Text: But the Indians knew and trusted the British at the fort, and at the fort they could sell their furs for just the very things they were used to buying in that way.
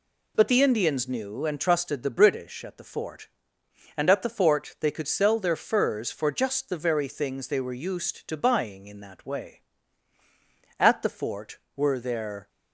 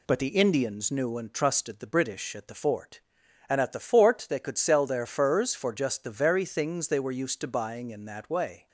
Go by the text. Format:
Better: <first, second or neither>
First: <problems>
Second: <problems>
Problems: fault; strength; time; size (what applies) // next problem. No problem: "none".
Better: second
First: goes on to say "At the fort were their"; strong; from 10.7 s on; 1.7 s long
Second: none